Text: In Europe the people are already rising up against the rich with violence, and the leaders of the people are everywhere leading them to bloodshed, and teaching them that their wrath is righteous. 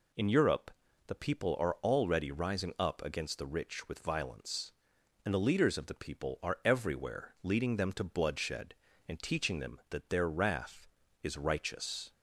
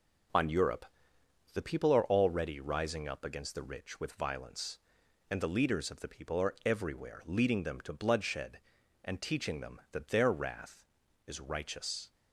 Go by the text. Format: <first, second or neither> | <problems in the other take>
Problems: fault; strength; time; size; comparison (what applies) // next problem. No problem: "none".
first | starts louder than the rest; noticeable; until 2.0 s; 6 dB // says "On" for "In"; at 0.3 s // pauses between "Europe" and "the"; noticeable; at 0.8 s; 0.70 s long; slight in the first